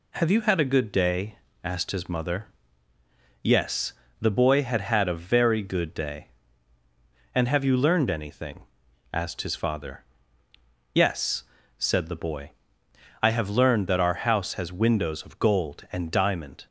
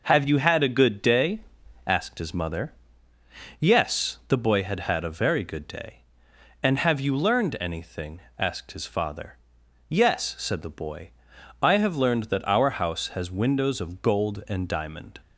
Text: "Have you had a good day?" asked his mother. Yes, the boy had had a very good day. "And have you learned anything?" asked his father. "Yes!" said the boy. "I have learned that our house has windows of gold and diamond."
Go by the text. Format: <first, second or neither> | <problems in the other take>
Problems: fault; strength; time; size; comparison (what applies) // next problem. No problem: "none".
neither | none